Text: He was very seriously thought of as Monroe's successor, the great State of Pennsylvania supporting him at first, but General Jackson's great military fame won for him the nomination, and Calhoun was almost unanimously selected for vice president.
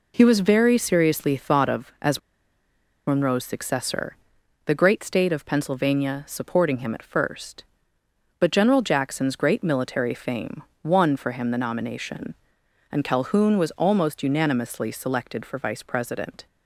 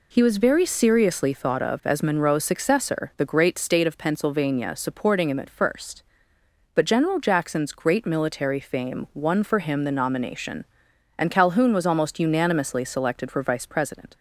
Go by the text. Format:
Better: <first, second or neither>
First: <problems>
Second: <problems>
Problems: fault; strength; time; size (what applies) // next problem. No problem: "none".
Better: second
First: pauses between "as" and "Monroe's"; noticeable; at 2.1 s; 0.88 s long // pauses between "fame" and "won"; slight; at 10.6 s; 0.22 s long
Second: none